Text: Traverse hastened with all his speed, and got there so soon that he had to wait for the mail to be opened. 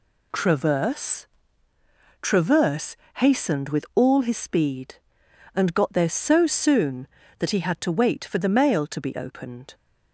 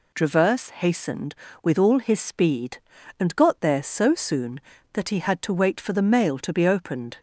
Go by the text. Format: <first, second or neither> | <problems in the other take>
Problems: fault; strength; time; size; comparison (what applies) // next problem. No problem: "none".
second | says "Traverse" twice; at 2.2 s